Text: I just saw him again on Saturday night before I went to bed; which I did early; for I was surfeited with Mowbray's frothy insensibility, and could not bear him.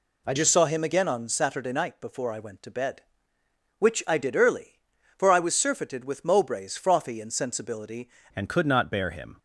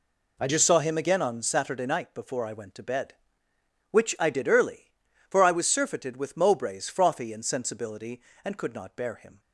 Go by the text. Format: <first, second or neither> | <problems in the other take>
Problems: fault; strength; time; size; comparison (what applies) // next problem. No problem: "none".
second | changes voice at "and"; from 8.3 s on; 1.0 s long